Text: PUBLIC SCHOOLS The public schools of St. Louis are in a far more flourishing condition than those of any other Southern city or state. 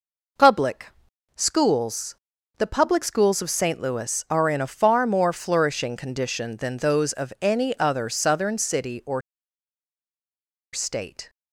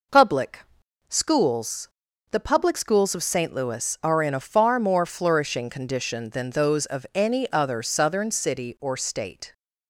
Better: second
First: pauses between "PUBLIC" and "SCHOOLS"; at 0.9 s; 0.44 s long // pauses between "SCHOOLS" and "The"; at 2.1 s; 0.44 s long // pauses between "or" and "state"; strong; at 9.2 s; 1.5 s long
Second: pauses between "PUBLIC" and "SCHOOLS"; at 0.6 s; 0.44 s long // pauses between "SCHOOLS" and "The"; at 1.8 s; 0.44 s long

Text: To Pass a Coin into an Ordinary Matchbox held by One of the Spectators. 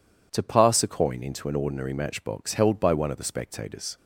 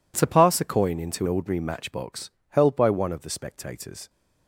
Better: first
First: none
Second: skips "an"; at 1.2 s // pauses between "Matchbox" and "held"; slight; at 2.2 s; 0.20 s long

